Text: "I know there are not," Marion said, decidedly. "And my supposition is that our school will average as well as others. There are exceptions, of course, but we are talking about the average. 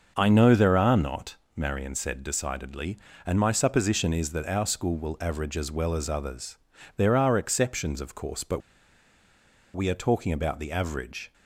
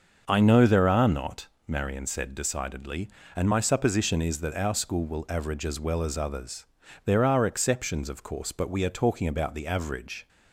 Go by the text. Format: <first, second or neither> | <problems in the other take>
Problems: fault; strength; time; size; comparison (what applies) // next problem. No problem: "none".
second | starts louder than the rest; until 1.1 s; 6 dB; also in the second // pauses between "but" and "we"; at 8.5 s; 1.1 s long